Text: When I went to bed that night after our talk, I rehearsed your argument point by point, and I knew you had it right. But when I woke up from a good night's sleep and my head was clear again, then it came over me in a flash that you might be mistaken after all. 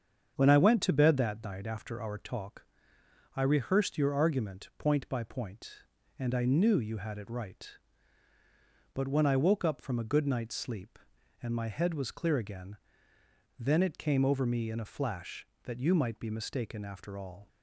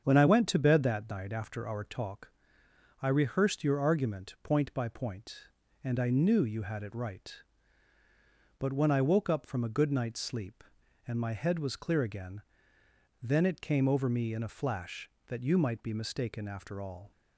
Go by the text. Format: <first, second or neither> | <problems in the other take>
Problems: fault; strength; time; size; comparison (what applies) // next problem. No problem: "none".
neither | starts louder than the rest; strong; the same in both